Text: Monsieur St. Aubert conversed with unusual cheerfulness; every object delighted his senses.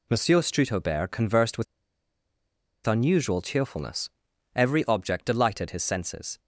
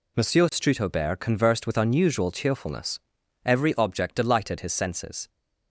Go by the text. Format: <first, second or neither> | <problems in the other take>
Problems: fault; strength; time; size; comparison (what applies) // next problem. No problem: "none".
second | pauses between "with" and "unusual"; at 1.6 s; 1.2 s long